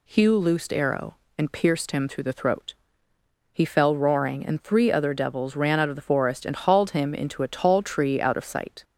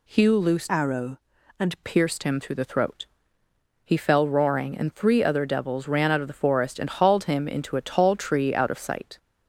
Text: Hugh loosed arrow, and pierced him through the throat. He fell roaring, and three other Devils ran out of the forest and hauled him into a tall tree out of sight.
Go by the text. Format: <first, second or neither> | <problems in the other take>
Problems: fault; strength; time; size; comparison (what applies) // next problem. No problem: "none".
first | changes voice from "arrow" to "and"; from 0.6 to 1.8 s; 1.2 s long